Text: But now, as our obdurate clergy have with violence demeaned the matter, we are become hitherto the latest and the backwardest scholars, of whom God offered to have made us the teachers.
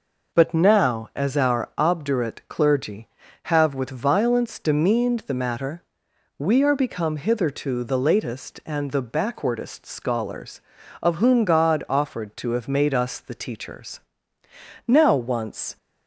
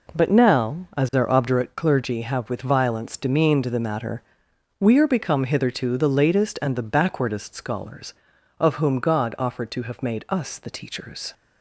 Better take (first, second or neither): second